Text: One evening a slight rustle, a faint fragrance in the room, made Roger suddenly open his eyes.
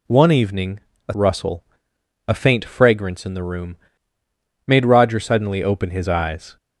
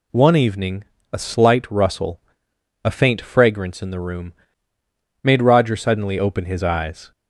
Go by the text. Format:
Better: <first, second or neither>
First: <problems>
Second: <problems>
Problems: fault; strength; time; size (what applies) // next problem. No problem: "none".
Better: second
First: pauses between "evening" and "a"; slight; at 0.7 s; 0.30 s long // skips "slight"; at 1.1 s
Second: pauses between "evening" and "a"; slight; at 0.8 s; 0.30 s long